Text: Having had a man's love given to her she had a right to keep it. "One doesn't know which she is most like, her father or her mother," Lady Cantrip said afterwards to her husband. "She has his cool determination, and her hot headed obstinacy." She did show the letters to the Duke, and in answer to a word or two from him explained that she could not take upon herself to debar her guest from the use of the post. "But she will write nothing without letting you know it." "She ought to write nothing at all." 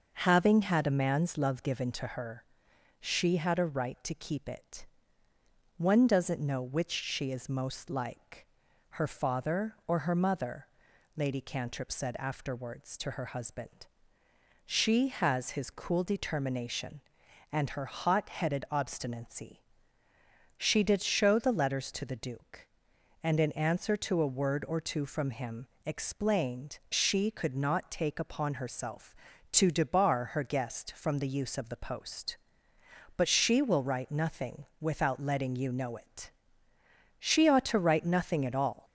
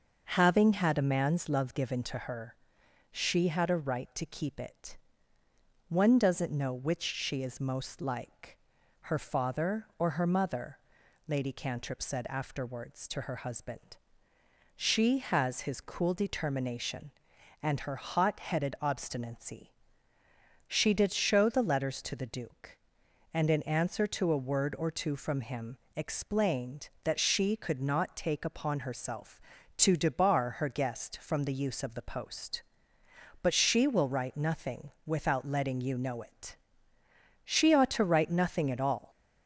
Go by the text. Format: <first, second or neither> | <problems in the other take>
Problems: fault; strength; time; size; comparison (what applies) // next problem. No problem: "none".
second | starts louder than the rest; noticeable; until 1.1 s; 6 dB; noticeable in the second // pauses between "her" and "she"; noticeable; at 2.4 s; 0.62 s long; noticeable in the second // pauses between "him" and "explained"; slight; at 25.6 s; 0.16 s long; slight in the second // skips "that"; at 26.8 s